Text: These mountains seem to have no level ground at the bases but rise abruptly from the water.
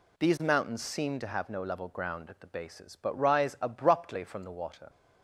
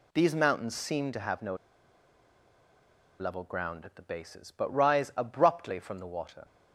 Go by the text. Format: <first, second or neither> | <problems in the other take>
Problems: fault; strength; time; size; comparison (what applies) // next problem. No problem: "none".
first | pauses between "no" and "level"; strong; at 1.5 s; 1.6 s long